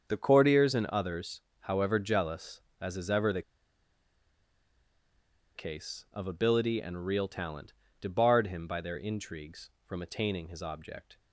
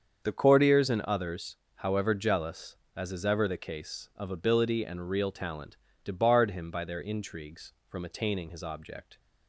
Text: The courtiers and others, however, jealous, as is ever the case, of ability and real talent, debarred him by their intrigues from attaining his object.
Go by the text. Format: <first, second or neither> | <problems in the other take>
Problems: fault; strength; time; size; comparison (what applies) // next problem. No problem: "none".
second | starts louder than the rest; until 1.0 s; 7 dB; also in the second // pauses between "the" and "case"; strong; at 3.4 s; 2.1 s long